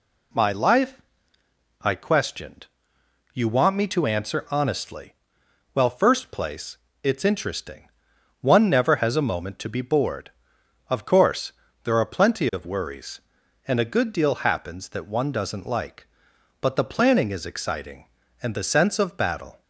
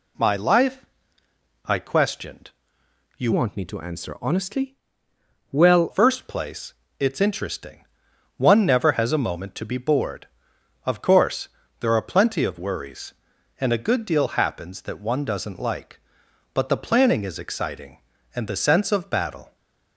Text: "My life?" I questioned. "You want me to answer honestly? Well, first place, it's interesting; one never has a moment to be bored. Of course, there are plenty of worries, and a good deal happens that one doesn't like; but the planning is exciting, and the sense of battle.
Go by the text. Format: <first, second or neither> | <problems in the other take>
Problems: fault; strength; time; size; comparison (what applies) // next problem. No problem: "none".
first | changes voice from "want" to "Well"; from 3.3 to 5.9 s; 2.6 s long